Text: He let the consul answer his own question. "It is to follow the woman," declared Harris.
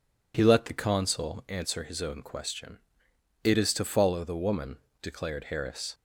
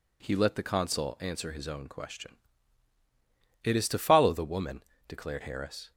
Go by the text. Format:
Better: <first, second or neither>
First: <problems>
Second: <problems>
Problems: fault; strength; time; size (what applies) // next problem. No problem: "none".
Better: neither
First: none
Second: none